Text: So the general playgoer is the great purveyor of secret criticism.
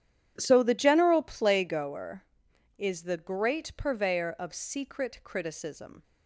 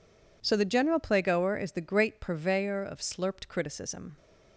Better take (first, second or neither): first